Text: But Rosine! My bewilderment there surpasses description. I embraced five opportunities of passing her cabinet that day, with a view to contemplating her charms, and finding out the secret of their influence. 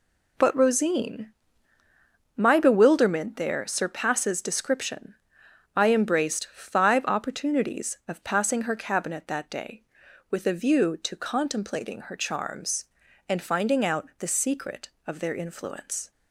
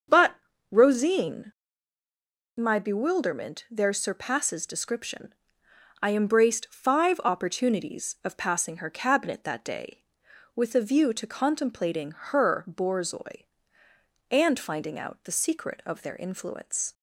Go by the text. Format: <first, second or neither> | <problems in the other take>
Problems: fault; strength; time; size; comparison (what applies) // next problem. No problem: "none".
first | starts louder than the rest; until 1.4 s; 6.5 dB // pauses between "But" and "Rosine"; slight; at 0.3 s; 0.36 s long // says "borzoi" for "charms"; at 12.6 s